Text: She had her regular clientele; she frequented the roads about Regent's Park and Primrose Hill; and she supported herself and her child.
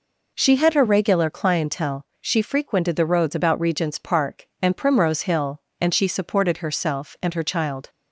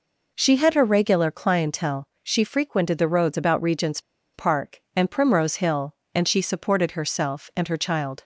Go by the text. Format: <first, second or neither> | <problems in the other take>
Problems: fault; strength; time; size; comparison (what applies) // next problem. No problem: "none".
first | pauses between "Regent's" and "Park"; slight; at 3.9 s; 0.34 s long